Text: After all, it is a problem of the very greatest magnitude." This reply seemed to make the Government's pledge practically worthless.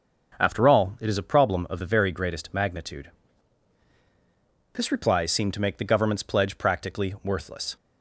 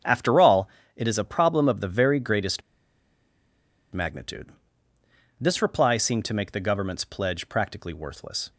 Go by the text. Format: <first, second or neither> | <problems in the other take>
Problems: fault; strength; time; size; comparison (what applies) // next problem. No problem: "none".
first | starts louder than the rest; strong; until 1.3 s; 7.5 dB // pauses between "greatest" and "magnitude"; strong; at 2.6 s; 1.3 s long